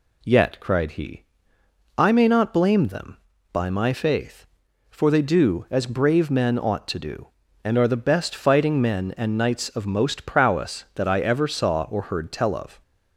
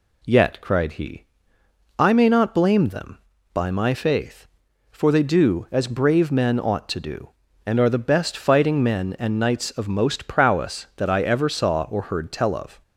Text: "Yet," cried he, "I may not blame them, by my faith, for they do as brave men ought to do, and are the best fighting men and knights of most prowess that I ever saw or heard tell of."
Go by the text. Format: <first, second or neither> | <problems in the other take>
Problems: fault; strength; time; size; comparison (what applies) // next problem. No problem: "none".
neither | none